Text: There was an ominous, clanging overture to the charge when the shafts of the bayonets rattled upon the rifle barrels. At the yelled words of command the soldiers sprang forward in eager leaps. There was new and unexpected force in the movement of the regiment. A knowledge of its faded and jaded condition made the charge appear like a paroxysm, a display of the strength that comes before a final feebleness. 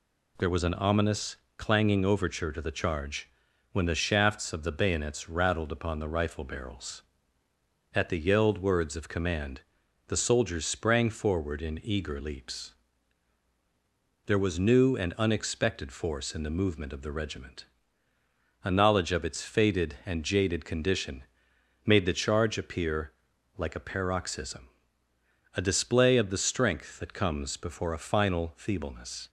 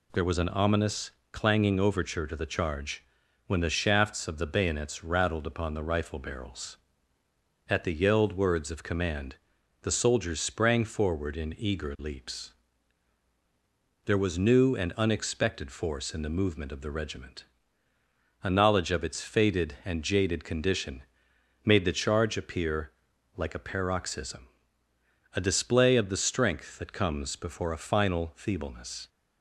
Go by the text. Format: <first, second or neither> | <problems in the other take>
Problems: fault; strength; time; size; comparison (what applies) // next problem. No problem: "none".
neither | pauses between "charge" and "when"; the same in both // pauses between "command" and "the"; noticeable; the same in both // pauses between "condition" and "made"; noticeable; the same in both // pauses between "appear" and "like"; the same in both